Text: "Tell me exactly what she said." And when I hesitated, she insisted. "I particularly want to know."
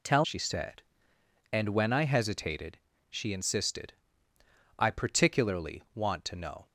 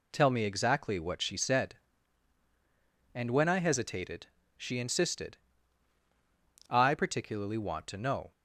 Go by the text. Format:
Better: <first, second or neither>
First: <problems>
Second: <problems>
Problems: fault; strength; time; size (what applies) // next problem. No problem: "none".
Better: second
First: skips "me exactly what"; at 0.2 s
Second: none